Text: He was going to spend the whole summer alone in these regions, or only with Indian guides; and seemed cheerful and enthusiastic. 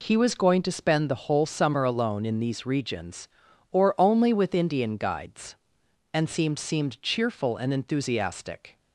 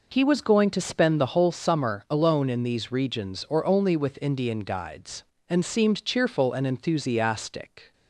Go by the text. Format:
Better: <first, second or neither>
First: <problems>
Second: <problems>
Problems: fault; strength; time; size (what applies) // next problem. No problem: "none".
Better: second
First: says "seemed" twice; at 6.5 s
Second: none